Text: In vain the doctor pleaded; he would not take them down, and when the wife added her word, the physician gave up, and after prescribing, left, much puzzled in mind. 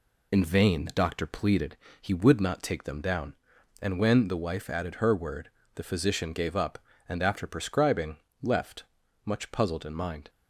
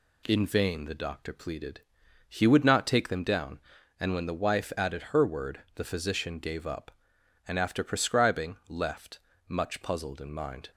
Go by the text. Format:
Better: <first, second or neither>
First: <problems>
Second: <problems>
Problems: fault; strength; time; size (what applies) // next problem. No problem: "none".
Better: second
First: loses the start of "In"; at 0.3 s; 40 ms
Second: none